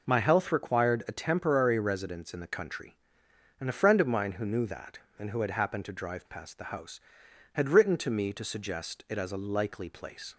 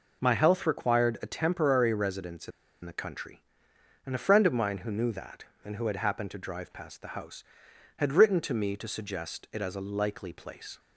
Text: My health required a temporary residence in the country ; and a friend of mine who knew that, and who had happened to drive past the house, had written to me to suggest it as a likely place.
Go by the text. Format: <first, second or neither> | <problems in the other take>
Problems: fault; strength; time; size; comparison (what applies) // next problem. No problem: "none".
first | pauses between "in" and "the"; slight; at 2.5 s; 0.34 s long